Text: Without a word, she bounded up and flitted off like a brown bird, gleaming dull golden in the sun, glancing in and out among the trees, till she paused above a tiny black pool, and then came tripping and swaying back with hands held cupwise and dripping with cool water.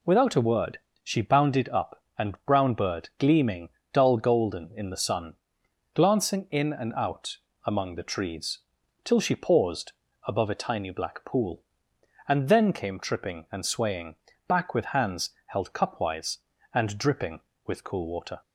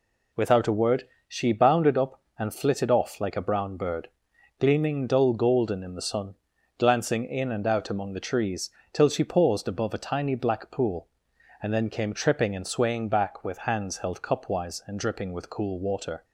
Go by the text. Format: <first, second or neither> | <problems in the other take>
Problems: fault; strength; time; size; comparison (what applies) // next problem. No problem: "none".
second | skips "flitted off like a"; at 2.4 s // pauses between "gleaming" and "dull"; slight; at 3.6 s; 0.24 s long // pauses between "out" and "among"; slight; at 7.3 s; 0.28 s long // pauses between "paused" and "above"; slight; at 9.9 s; 0.34 s long // pauses between "swaying" and "back"; slight; at 14.1 s; 0.32 s long // pauses between "hands" and "held"; slight; at 15.2 s; 0.18 s long